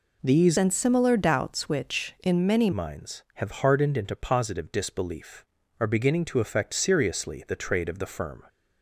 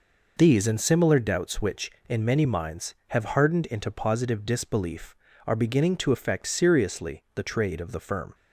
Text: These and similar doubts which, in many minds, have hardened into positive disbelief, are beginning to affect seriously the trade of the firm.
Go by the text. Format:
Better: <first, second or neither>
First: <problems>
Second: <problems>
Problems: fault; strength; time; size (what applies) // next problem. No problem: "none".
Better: second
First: changes voice from "and" to "many"; from 0.5 to 2.7 s; 2.2 s long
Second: none